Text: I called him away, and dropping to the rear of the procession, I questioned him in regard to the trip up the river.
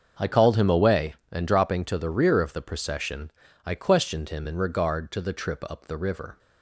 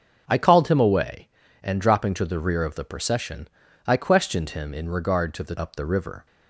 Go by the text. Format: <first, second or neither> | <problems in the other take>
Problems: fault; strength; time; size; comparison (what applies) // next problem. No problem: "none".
first | starts louder than the rest; until 1.2 s; 6.5 dB; also in the first // skips "trip"; at 5.5 s